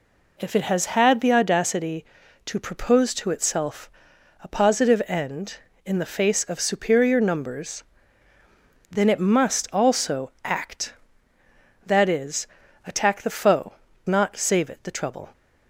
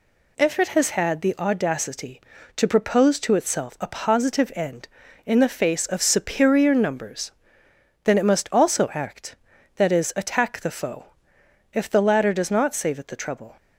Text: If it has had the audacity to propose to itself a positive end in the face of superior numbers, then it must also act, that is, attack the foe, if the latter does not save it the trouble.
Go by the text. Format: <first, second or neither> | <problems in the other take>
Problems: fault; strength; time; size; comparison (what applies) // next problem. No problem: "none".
second | pauses between "itself" and "a"; noticeable; at 3.8 s; 0.54 s long // skips "if the latter does"; at 13.8 s